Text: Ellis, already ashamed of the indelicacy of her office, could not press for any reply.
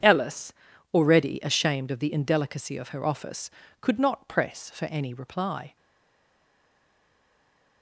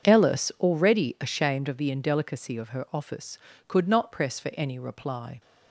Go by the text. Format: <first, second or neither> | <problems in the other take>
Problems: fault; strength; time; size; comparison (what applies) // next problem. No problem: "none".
second | stays silent after the last word; noticeable; from 5.7 s on; 2.1 s long